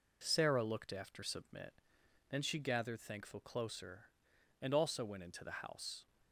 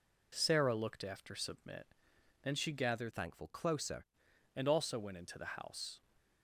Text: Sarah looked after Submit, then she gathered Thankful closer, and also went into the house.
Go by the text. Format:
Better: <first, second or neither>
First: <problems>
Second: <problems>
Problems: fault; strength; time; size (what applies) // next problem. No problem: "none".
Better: first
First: none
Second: changes voice from "Thankful" to "closer"; from 3.1 to 4.0 s; 0.9 s long